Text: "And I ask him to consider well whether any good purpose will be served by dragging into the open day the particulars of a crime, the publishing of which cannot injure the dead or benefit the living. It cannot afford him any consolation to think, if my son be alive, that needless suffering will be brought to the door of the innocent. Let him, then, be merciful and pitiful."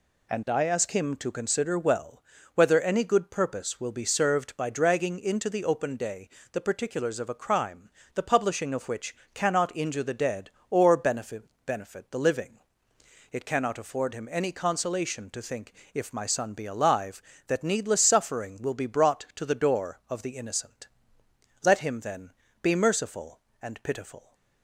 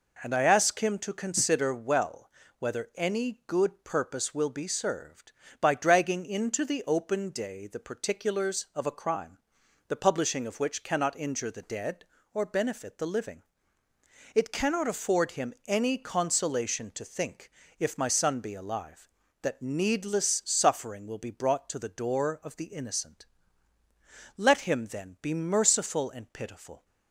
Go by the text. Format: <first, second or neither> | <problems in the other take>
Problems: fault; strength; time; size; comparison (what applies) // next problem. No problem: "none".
second | pauses between "well" and "whether"; slight; at 2.2 s; 0.32 s long; slight in the second // pauses between "day" and "the"; slight; at 6.2 s; 0.22 s long // pauses between "which" and "cannot"; slight; at 9.1 s; 0.18 s long // says "benefit" twice; at 11.6 s